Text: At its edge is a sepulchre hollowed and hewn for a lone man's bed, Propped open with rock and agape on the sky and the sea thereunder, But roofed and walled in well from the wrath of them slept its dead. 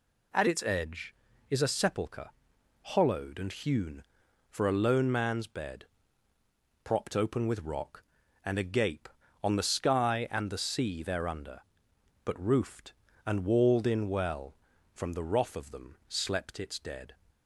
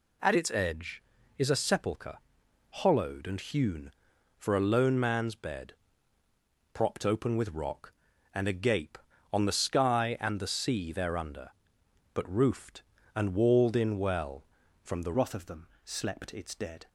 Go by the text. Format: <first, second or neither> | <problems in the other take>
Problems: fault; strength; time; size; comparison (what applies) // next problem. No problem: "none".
first | pauses between "sepulchre" and "hollowed"; noticeable; at 2.1 s; 0.50 s long; noticeable in the first // changes voice at "wrath"; from 15.1 s on; 1.7 s long // pauses between "them" and "slept"; slight; at 15.6 s; 0.18 s long